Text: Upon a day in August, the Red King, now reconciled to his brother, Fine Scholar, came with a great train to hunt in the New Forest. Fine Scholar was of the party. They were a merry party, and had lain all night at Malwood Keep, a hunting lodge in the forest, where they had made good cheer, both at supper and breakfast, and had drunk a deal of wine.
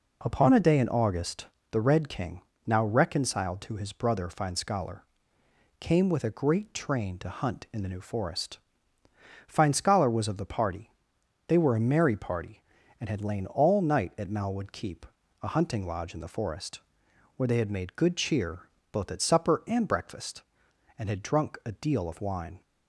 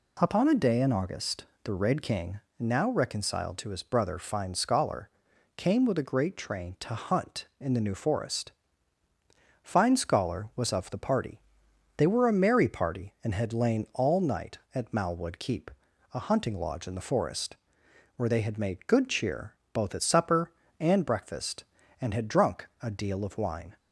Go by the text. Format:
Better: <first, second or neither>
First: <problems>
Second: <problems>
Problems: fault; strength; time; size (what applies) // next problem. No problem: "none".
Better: neither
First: none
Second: none